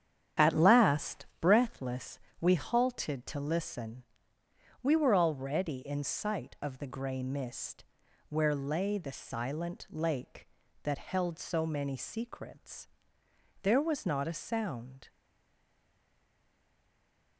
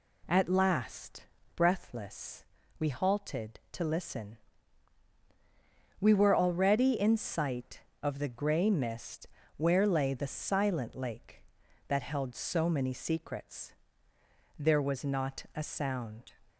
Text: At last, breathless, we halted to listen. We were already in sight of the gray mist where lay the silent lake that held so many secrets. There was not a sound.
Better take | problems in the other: second | starts louder than the rest; strong; until 1.5 s; 9 dB // pauses between "mist" and "where"; noticeable; at 7.8 s; 0.46 s long; slight in the second // stays silent after the last word; from 15.0 s on; 2.3 s long

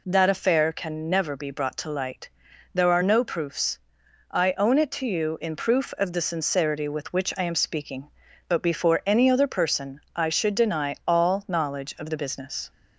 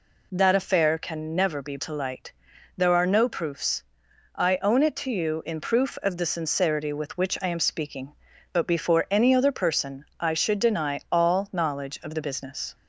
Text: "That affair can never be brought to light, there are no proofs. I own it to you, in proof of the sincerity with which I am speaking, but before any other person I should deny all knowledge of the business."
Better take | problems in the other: first | skips "brought"; at 1.7 s

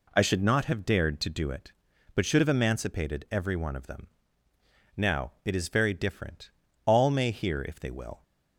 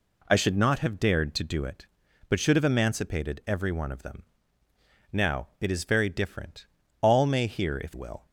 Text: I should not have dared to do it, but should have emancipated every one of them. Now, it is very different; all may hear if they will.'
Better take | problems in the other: first | skips "they"; at 7.9 s

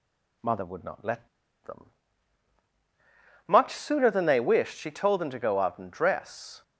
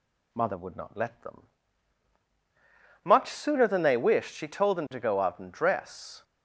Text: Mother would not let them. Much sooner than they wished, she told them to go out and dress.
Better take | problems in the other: second | pauses between "let" and "them"; at 1.2 s; 0.38 s long

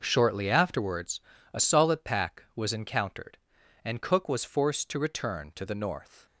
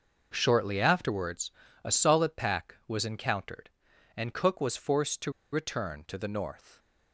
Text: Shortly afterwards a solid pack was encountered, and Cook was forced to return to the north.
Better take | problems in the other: first | pauses between "afterwards" and "a"; slight; at 1.5 s; 0.34 s long; slight in the first // pauses between "to" and "return"; slight; at 5.3 s; 0.22 s long

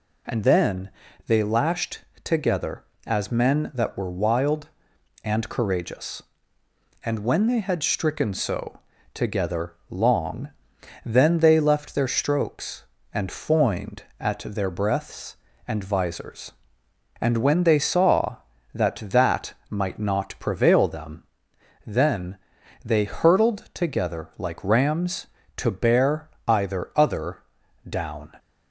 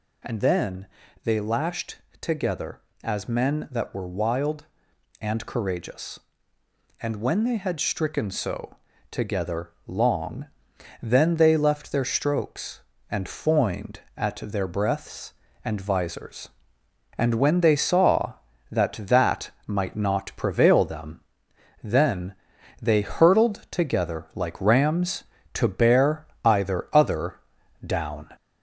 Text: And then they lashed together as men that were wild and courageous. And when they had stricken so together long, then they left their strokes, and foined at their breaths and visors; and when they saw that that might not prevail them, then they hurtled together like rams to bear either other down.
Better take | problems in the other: first | gets louder; slight; throughout; 3 dB // pauses between "then" and "they"; at 0.8 s; 0.38 s long; also in the first // pauses between "lashed" and "together"; slight; at 1.9 s; 0.22 s long; slight in the first // pauses between "so" and "together"; slight; at 8.7 s; 0.34 s long; slight in the first // pauses between "together" and "long"; slight; at 9.7 s; 0.16 s long; slight in the first // pauses between "that" and "might"; slight; at 19.5 s; 0.16 s long; slight in the first // pauses between "then" and "they"; noticeable; at 22.3 s; 0.46 s long; noticeable in the first // pauses between "bear" and "either"; slight; at 26.2 s; 0.18 s long; slight in the first // pauses between "other" and "down"; noticeable; at 27.3 s; 0.50 s long; noticeable in the first

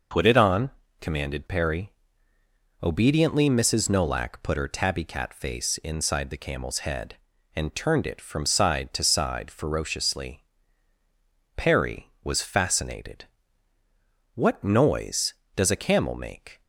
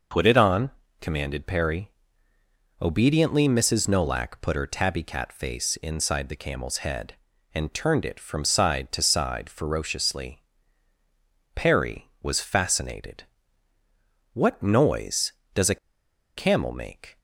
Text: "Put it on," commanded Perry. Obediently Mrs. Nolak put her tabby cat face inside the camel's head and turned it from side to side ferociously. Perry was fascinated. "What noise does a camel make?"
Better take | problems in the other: first | pauses between "a" and "camel"; noticeable; at 15.7 s; 0.59 s long

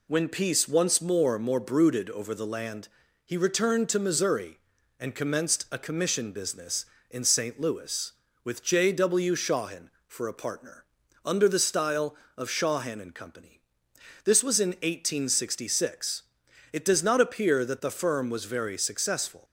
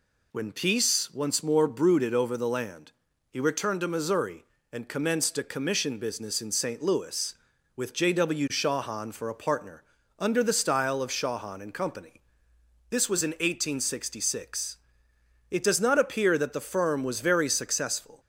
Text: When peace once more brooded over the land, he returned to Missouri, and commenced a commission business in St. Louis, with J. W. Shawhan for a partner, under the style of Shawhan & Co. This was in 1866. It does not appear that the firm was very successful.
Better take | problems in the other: second | says "more" twice; at 1.3 s

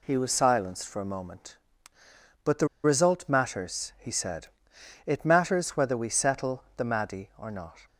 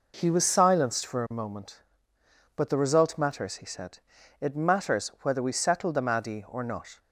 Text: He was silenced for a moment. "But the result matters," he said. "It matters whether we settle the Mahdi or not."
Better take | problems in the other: second | pauses between "the" and "result"; slight; at 2.6 s; 0.18 s long

